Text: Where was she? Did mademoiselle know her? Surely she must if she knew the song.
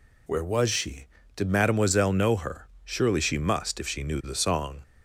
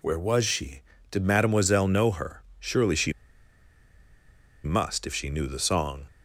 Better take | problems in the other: first | pauses between "she" and "must"; strong; at 3.1 s; 1.5 s long

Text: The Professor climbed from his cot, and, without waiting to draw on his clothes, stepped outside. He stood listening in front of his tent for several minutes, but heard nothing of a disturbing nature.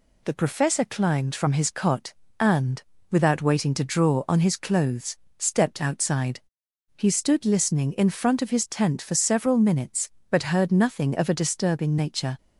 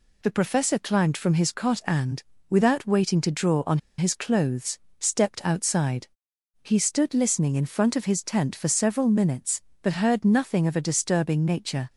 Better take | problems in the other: first | pauses between "on" and "his"; slight; at 3.7 s; 0.19 s long

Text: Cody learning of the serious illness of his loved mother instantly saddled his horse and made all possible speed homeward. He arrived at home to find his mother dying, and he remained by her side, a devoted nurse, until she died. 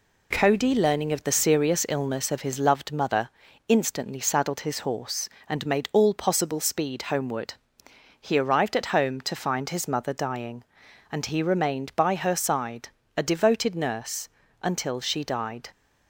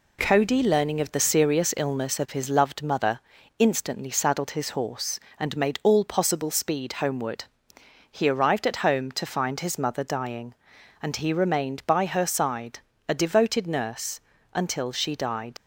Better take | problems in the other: first | pauses between "mother" and "instantly"; at 3.1 s; 0.40 s long; also in the first // leaves "died" unfinished; at 15.5 s; 50 ms

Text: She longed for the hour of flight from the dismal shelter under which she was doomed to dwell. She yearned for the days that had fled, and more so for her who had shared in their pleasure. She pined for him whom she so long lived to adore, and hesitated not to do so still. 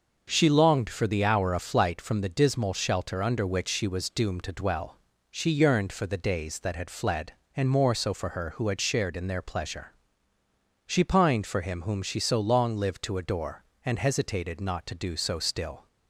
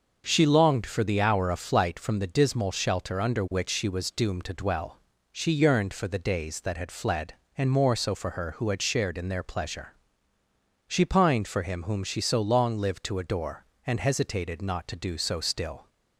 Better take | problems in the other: neither | starts louder than the rest; noticeable; the same in both

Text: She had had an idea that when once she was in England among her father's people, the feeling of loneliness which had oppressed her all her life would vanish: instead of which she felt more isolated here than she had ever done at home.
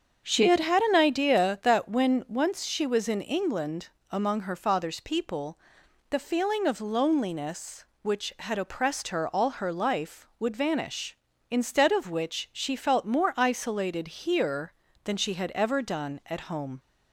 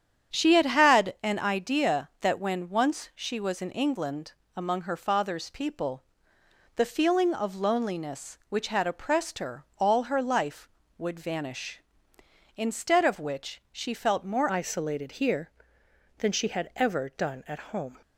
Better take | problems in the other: first | starts louder than the rest; strong; until 1.4 s; 9 dB; strong in the first // pauses between "England" and "among"; slight; at 4.3 s; 0.24 s long; slight in the first // changes voice at "isolated"; from 14.4 s on; 3.5 s long // pauses between "at" and "home"; slight; at 17.5 s; 0.16 s long

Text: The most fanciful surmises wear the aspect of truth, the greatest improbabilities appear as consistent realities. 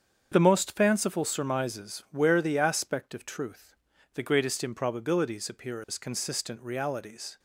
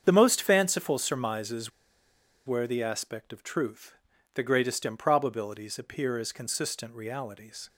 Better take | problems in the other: first | starts louder than the rest; strong; until 1.0 s; 7.5 dB; strong in the first // pauses between "surmises" and "wear"; noticeable; at 1.7 s; 0.75 s long

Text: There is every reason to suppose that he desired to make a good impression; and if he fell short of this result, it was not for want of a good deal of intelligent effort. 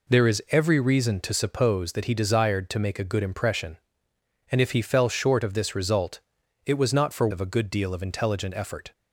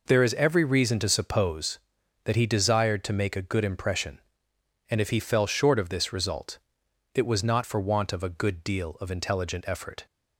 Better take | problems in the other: second | skips "want"; at 7.2 s

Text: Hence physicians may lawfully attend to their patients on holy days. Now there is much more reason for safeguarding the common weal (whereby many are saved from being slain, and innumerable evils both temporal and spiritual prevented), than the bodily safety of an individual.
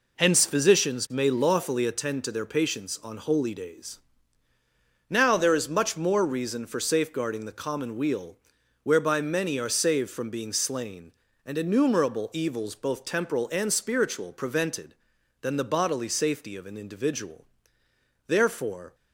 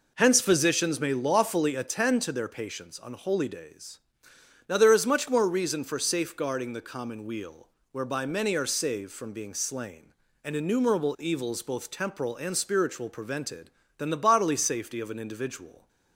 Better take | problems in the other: second | goes on to say "Therefore"; noticeable; from 18.2 s on; 0.68 s long

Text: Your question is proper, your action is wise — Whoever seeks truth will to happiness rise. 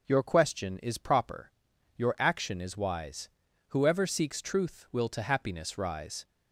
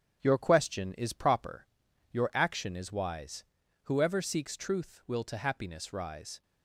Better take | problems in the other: first | gets quieter; noticeable; throughout; 5 dB // starts louder than the rest; strong; until 1.2 s; 9 dB; noticeable in the first

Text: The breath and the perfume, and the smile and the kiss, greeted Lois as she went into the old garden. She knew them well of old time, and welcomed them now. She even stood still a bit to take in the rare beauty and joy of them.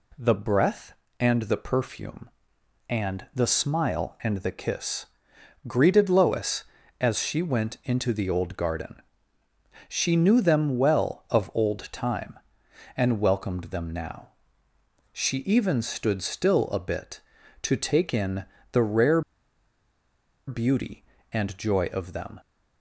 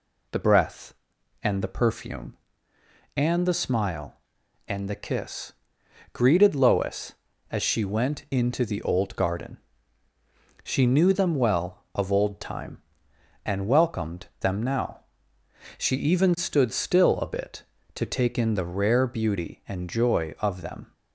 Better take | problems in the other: second | pauses between "in" and "the"; slight; at 18.4 s; 0.28 s long // pauses between "rare" and "beauty"; strong; at 19.2 s; 1.2 s long

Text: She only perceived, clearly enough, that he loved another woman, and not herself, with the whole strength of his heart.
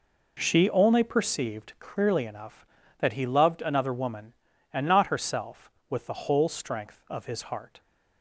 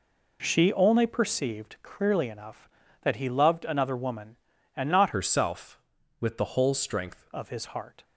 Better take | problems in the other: first | changes voice from "herself" to "strength"; from 5.1 to 7.2 s; 2.1 s long

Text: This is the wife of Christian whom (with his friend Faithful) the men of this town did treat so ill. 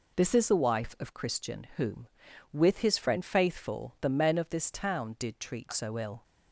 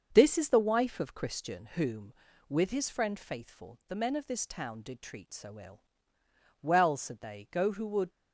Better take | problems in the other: first | starts louder than the rest; until 1.1 s; 6.5 dB // goes on to say "Well said they go who would"; from 6.6 s on; 1.4 s long

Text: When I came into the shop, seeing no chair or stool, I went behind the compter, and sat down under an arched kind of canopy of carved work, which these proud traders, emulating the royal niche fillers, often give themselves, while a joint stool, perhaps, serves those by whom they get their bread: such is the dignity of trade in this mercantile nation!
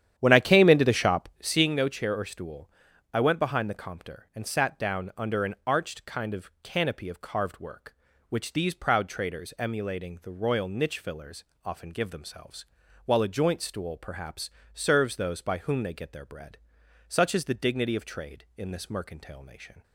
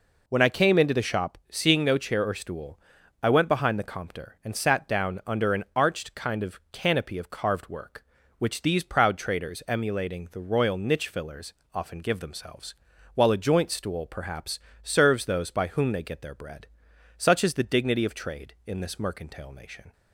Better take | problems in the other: second | starts louder than the rest; strong; until 1.6 s; 10 dB

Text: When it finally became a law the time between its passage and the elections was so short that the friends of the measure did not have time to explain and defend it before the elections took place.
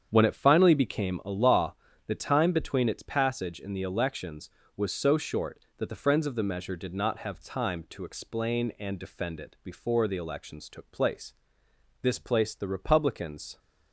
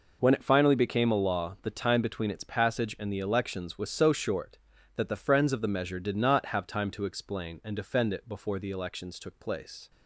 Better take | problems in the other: second | starts louder than the rest; strong; until 1.1 s; 8 dB // pauses between "law" and "the"; slight; at 1.7 s; 0.32 s long // goes on to say "This placed the Republicans"; from 12.0 s on; 1.5 s long

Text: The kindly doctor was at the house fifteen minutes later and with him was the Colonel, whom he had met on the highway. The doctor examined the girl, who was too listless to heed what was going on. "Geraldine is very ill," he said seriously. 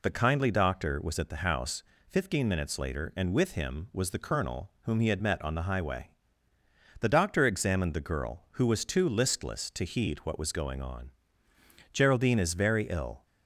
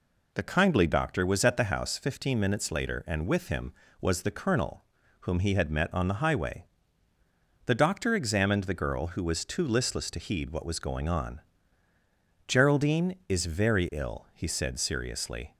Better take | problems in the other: second | pauses between "house" and "fifteen"; slight; at 1.8 s; 0.26 s long // stops before "he said seriously"; at 13.2 s

